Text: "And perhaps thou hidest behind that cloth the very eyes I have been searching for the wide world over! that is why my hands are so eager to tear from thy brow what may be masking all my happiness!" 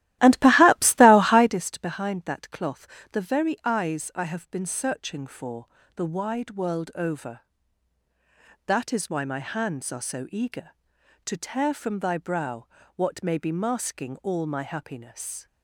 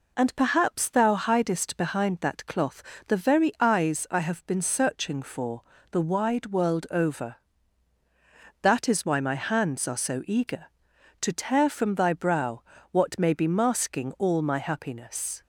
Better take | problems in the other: second | starts louder than the rest; strong; until 1.6 s; 15 dB // pauses between "cloth" and "the"; slight; at 2.8 s; 0.26 s long; slight in the second // pauses between "for" and "the"; slight; at 5.6 s; 0.28 s long; slight in the second // pauses between "brow" and "what"; slight; at 12.6 s; 0.30 s long; slight in the second

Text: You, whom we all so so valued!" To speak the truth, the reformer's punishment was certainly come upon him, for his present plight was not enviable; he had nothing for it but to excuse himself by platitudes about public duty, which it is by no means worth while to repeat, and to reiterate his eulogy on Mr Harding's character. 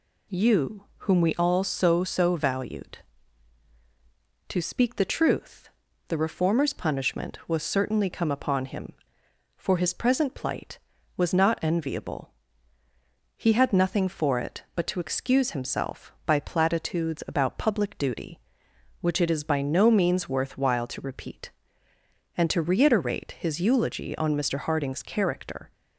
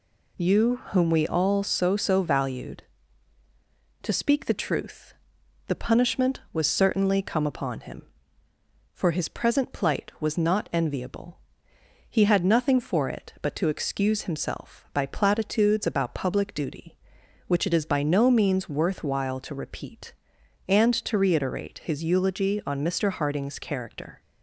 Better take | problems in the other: first | skips "reformer's"; at 5.7 s

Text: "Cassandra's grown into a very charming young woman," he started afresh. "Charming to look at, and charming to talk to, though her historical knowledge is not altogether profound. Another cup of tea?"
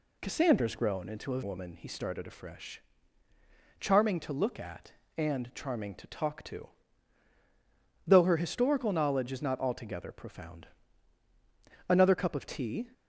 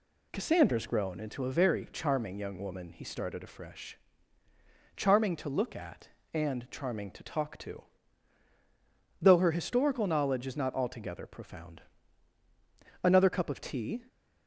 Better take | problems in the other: second | skips "very charming young"; at 1.4 s

